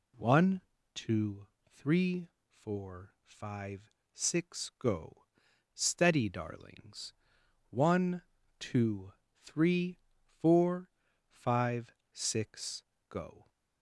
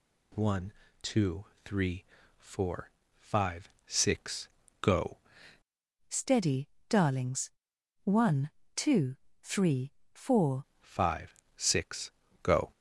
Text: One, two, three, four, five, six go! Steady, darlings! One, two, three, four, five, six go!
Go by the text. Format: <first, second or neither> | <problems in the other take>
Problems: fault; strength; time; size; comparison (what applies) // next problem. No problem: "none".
first | pauses between "six" and "go"; slight; at 4.4 s; 0.34 s long // changes voice from "Steady" to "four"; from 6.0 to 10.6 s; 4.6 s long // pauses between "six" and "go"; slight; at 12.0 s; 0.32 s long; slight in the first